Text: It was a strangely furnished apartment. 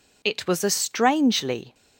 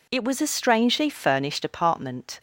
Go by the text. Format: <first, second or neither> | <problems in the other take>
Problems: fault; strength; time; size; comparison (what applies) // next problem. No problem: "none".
second | stops before "furnished apartment"; at 1.7 s